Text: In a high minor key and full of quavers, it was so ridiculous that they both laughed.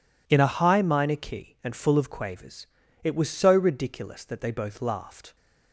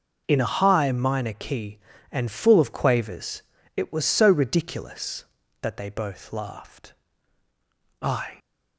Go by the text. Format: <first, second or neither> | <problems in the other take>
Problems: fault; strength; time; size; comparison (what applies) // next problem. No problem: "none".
first | goes on to say "I"; slight; from 8.0 s on; 0.38 s long